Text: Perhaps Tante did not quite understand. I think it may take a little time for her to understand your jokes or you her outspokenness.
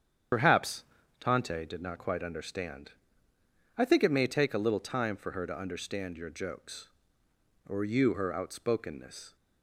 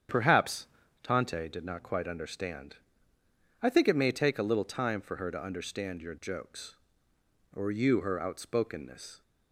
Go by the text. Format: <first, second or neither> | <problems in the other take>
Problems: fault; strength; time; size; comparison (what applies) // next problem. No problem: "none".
second | loses the start of "Perhaps"; at 0.3 s; 60 ms // starts louder than the rest; strong; until 1.7 s; 8.5 dB; strong in the second // pauses between "Perhaps" and "Tante"; at 0.8 s; 0.38 s long; also in the second